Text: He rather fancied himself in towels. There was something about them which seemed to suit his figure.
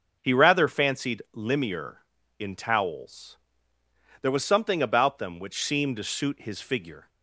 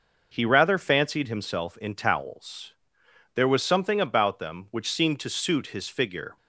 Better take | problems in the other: second | starts louder than the rest; until 1.2 s; 7 dB // says "limier" for "himself"; at 1.3 s

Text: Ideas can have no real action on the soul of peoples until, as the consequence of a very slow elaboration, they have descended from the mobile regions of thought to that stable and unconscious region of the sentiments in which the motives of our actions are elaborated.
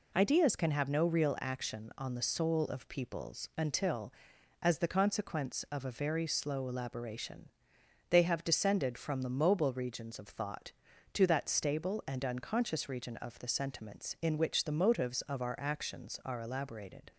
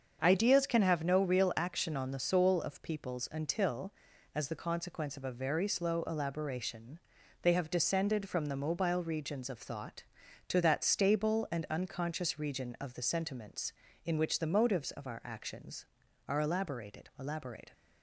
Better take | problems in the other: first | starts louder than the rest; until 1.2 s; 7 dB // says "elaborated" twice; at 17.1 s

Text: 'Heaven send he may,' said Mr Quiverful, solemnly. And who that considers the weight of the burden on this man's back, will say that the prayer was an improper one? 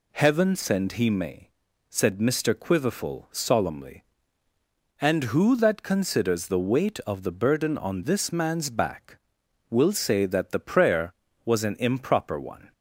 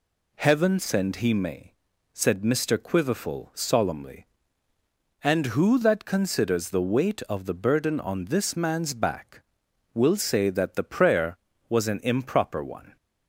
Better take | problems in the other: neither | none

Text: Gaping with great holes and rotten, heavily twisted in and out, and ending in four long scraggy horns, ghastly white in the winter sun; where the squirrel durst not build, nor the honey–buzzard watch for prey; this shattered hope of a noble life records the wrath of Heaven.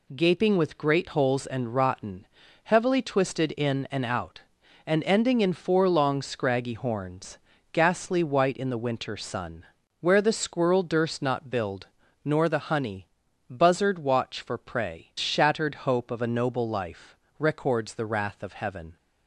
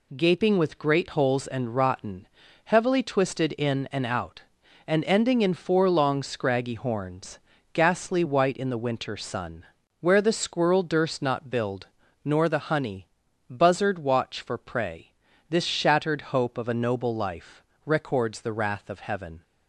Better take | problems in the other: second | skips "this"; at 15.1 s // pauses between "life" and "records"; slight; at 17.1 s; 0.24 s long; slight in the second

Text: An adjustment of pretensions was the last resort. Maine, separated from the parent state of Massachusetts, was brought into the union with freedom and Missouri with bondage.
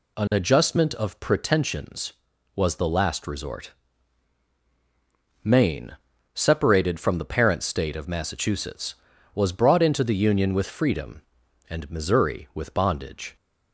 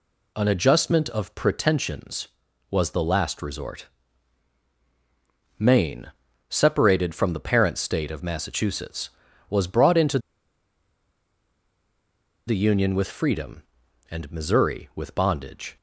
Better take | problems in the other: first | pauses between "into" and "the"; strong; at 10.2 s; 2.2 s long

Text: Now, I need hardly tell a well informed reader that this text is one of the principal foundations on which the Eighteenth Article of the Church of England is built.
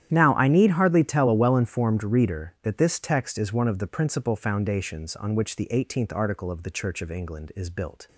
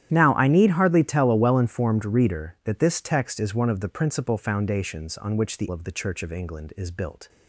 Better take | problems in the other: first | starts louder than the rest; strong; until 1.1 s; 11.5 dB; strong in the first // skips "Eighteenth Article"; at 5.6 s

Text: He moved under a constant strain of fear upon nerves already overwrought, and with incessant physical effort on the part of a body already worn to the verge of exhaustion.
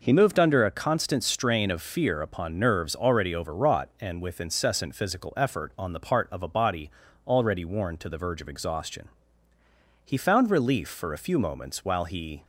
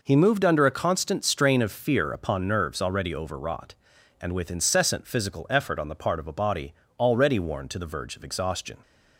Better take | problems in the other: second | pauses between "body" and "already"; slight; at 6.8 s; 0.34 s long; slight in the second // goes on to say "He found relief for a few moments while he"; strong; from 10.0 s on; 2.4 s long

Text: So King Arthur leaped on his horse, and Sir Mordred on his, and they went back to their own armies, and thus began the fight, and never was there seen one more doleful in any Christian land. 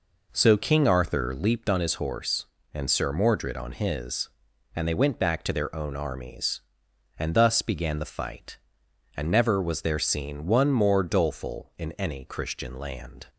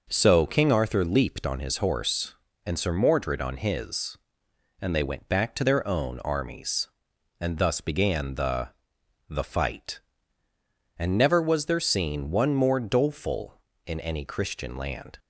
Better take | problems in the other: first | says "the" twice; at 9.2 s

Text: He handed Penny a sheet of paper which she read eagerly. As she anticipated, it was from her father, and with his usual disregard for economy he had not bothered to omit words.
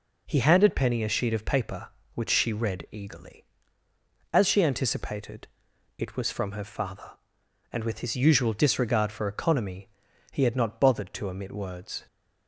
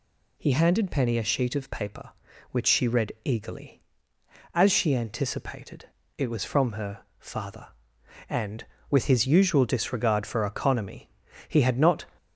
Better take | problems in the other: first | pauses between "her" and "father"; slight; at 7.0 s; 0.16 s long // pauses between "economy" and "he"; at 11.0 s; 0.38 s long; also in the first // stops before "bothered to omit words"; at 12.1 s

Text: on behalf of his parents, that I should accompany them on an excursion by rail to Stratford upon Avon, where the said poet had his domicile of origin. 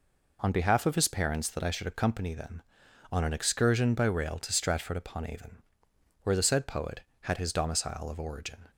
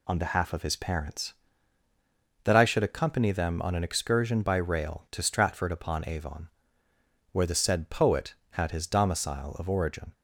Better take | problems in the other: neither | none

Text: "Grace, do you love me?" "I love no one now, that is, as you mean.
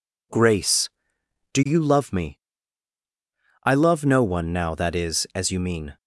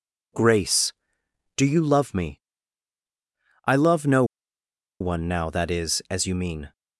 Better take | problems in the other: first | pauses between "no" and "one"; noticeable; at 4.2 s; 0.76 s long

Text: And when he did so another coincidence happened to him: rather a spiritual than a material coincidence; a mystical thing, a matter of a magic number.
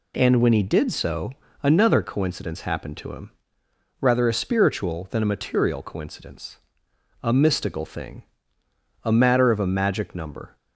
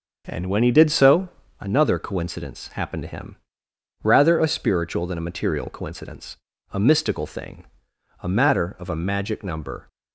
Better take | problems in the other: first | starts louder than the rest; until 1.7 s; 6.5 dB // pauses between "so" and "another"; slight; at 1.2 s; 0.32 s long; slight in the first

